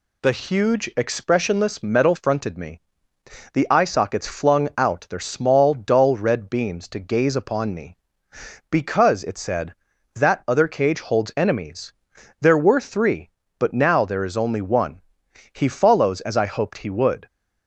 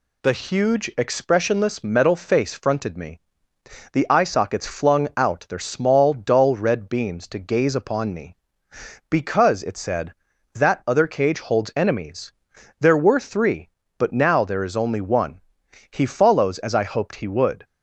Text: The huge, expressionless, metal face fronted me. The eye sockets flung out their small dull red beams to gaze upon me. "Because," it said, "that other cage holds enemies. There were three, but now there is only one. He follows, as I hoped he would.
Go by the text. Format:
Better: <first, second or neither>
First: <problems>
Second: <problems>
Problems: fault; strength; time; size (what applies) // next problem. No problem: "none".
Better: second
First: skips "face"; at 2.1 s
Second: none